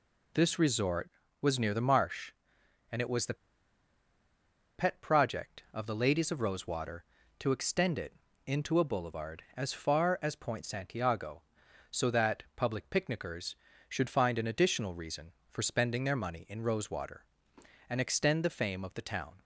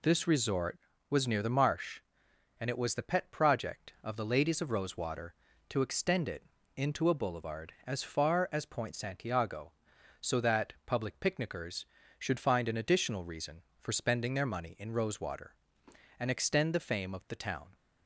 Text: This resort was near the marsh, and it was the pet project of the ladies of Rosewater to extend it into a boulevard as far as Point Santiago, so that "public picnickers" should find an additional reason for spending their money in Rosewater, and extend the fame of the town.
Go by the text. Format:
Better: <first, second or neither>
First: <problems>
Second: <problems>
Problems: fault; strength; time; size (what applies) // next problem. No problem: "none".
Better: second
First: pauses between "the" and "pet"; strong; at 3.3 s; 1.4 s long // pauses between "it" and "into"; slight; at 8.1 s; 0.32 s long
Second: pauses between "it" and "into"; slight; at 6.4 s; 0.32 s long